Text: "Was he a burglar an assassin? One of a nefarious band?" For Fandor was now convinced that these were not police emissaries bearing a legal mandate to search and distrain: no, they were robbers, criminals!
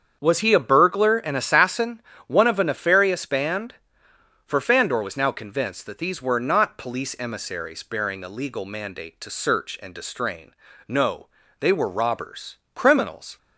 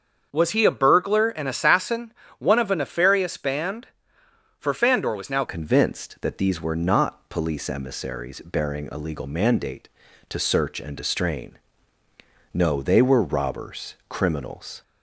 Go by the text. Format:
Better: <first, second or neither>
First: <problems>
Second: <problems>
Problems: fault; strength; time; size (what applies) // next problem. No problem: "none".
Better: first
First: starts louder than the rest; strong; until 1.2 s; 7.5 dB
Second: starts louder than the rest; until 1.3 s; 7 dB // changes voice at "convinced"; from 5.4 s on; 9.4 s long